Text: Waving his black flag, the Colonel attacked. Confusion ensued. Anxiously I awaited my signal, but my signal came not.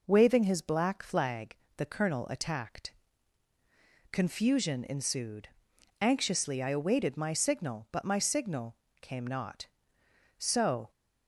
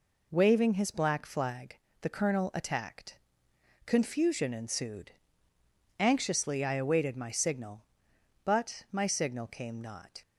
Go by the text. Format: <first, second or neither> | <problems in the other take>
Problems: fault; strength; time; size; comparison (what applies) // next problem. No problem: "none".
second | pauses between "signal" and "came"; slight; at 8.7 s; 0.26 s long // goes on to say "So"; from 10.3 s on; 0.52 s long